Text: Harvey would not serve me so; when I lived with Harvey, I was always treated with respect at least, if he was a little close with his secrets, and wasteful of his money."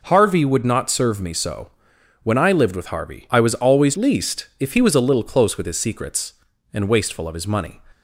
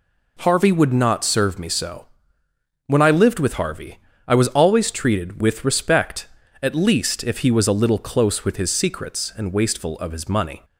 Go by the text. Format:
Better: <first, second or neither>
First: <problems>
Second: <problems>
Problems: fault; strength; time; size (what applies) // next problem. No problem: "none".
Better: second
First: skips "treated with respect at"; at 3.9 s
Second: none